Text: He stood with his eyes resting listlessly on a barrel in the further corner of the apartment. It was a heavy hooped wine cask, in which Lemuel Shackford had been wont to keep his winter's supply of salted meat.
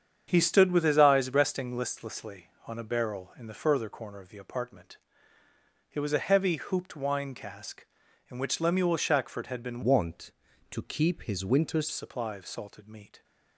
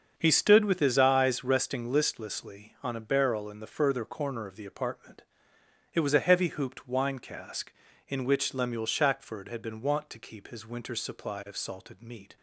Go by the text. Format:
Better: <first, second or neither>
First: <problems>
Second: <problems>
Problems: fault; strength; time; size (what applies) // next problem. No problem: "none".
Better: second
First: starts louder than the rest; strong; until 1.2 s; 7.5 dB // changes voice from "wont" to "winter's"; from 9.8 to 11.8 s; 2.0 s long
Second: starts louder than the rest; until 1.1 s; 6.5 dB